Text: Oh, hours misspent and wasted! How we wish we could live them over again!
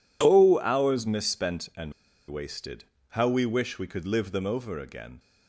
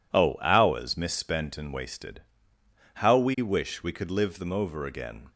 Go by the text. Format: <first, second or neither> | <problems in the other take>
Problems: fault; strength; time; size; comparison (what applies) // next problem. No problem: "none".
second | pauses between "and" and "wasted"; at 1.9 s; 0.36 s long